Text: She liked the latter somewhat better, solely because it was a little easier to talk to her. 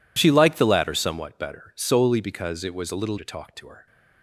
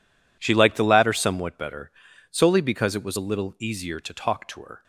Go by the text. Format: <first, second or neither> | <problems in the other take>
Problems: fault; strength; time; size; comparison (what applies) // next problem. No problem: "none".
second | skips "easier"; at 3.1 s